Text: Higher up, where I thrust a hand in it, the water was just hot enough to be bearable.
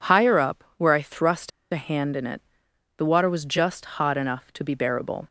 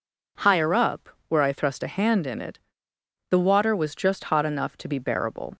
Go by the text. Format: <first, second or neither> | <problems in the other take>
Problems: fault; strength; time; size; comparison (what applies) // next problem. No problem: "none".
second | pauses between "thrust" and "a"; slight; at 1.5 s; 0.22 s long